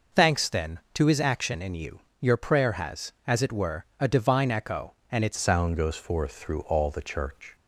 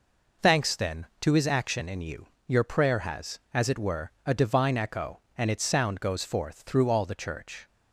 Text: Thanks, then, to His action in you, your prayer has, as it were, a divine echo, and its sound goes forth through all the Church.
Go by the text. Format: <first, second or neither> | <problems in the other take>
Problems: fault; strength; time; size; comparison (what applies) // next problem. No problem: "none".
second | changes voice at "sound"; from 5.3 s on; 2.2 s long